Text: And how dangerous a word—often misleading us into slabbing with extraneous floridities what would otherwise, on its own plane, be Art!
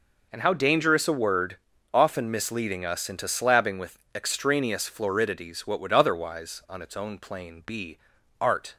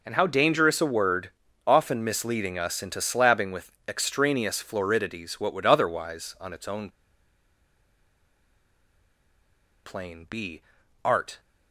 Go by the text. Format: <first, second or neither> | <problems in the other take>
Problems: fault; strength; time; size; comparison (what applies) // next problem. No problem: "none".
first | pauses between "with" and "extraneous"; slight; at 3.7 s; 0.16 s long; slight in the first // pauses between "own" and "plane"; strong; at 6.8 s; 2.9 s long // pauses between "be" and "Art"; at 10.6 s; 0.42 s long; also in the first